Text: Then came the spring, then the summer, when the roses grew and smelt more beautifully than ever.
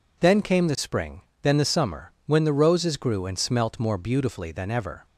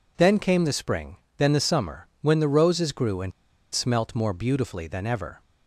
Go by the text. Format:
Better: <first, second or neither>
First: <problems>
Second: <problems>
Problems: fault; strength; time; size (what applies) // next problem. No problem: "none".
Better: first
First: none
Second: pauses between "and" and "smelt"; at 3.3 s; 0.41 s long